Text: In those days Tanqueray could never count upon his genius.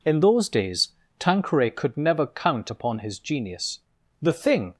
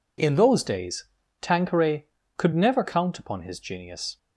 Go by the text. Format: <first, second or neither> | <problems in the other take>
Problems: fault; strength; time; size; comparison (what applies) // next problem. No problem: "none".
second | pauses between "days" and "Tanqueray"; slight; at 0.8 s; 0.30 s long; slight in the second // goes on to say "The thing"; from 4.2 s on; 0.54 s long